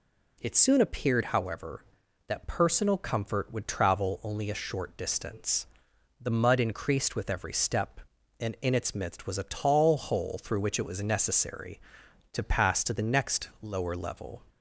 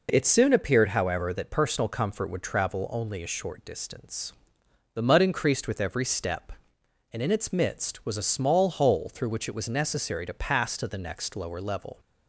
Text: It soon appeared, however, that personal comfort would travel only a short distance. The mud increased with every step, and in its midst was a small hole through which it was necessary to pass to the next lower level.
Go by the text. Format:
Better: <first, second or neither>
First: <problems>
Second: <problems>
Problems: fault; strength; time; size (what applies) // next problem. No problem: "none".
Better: second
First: says "tall" for "small"; at 9.4 s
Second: none